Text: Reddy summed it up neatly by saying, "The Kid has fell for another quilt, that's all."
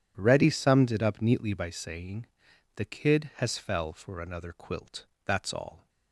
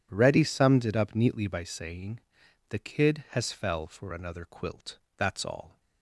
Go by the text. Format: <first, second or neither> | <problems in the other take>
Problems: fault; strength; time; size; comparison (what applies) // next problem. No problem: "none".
neither | none